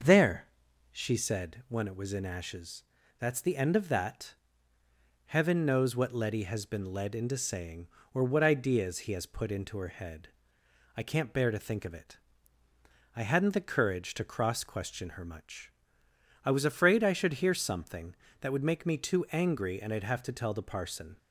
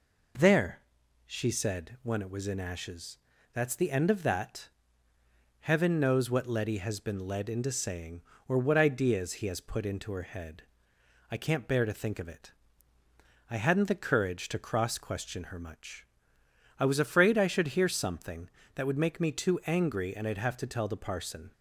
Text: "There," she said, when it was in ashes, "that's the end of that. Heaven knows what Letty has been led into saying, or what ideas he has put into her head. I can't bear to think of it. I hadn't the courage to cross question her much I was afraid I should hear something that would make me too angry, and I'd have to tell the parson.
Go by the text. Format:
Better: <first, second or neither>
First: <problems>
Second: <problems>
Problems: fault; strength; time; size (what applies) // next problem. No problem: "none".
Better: second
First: starts louder than the rest; until 1.2 s; 6.5 dB // pauses between "much" and "I"; noticeable; at 15.6 s; 0.74 s long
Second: pauses between "much" and "I"; noticeable; at 16.0 s; 0.74 s long